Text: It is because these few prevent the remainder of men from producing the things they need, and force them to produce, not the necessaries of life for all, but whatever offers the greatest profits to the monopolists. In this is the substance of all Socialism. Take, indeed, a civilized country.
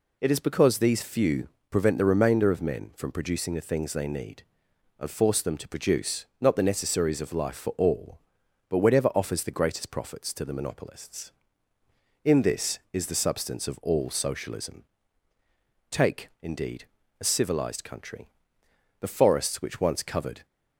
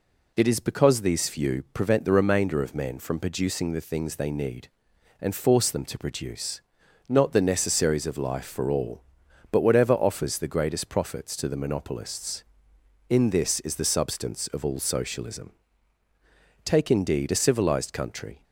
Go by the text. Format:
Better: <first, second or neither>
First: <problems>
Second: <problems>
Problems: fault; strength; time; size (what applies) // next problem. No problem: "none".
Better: second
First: pauses between "few" and "prevent"; slight; at 1.4 s; 0.22 s long // goes on to say "The forests which once covered"; from 18.9 s on; 1.4 s long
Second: none